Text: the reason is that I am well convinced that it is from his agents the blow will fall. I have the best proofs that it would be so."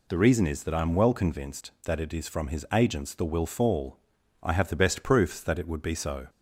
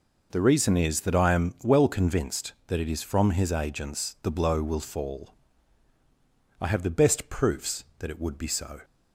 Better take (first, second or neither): second